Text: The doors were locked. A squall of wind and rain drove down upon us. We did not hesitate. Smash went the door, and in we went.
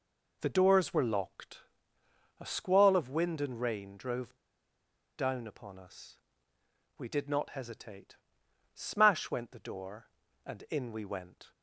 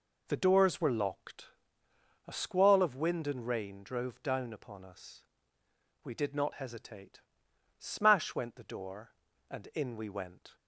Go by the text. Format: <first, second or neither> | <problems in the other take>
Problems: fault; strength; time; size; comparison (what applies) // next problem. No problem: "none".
second | pauses between "drove" and "down"; noticeable; at 4.3 s; 0.80 s long